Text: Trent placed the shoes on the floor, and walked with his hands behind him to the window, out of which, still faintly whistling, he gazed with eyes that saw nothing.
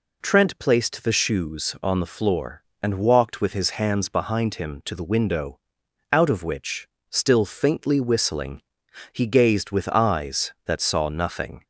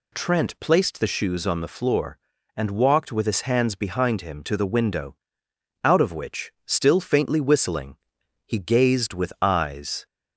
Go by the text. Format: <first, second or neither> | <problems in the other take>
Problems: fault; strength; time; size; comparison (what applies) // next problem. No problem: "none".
first | stops before "that saw nothing"; at 10.0 s